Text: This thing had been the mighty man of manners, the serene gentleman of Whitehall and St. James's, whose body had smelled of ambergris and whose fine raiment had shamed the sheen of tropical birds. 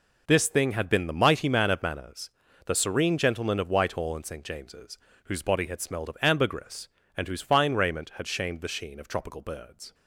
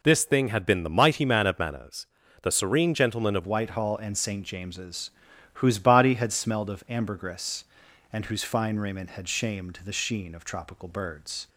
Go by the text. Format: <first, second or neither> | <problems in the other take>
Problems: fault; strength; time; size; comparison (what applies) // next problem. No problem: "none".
first | changes voice at "Whitehall"; from 3.4 s on; 8.0 s long